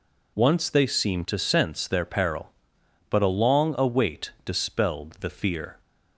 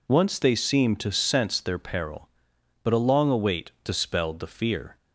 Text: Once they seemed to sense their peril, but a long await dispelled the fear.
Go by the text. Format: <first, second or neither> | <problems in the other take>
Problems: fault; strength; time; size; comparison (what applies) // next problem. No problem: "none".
neither | none